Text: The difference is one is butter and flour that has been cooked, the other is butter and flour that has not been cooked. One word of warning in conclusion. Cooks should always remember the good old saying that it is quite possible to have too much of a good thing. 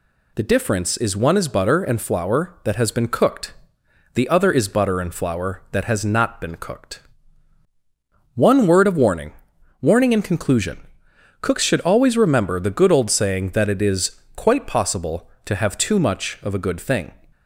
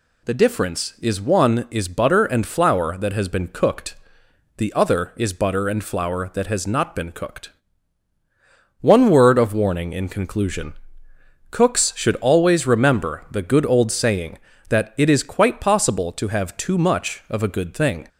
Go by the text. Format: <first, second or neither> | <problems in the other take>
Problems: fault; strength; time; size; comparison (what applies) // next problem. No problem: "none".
second | says "warning" twice; at 9.7 s